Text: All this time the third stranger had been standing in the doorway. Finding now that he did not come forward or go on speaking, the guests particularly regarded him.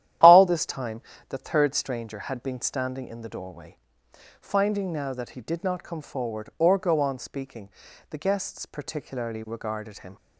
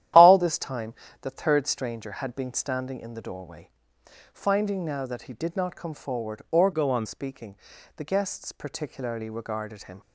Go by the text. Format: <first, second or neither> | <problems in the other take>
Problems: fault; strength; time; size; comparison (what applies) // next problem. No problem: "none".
first | starts louder than the rest; strong; until 1.4 s; 12 dB; strong in the first // pauses between "time" and "the"; slight; at 0.9 s; 0.28 s long; slight in the first // changes voice from "go" to "on"; from 6.7 to 7.0 s; 0.3 s long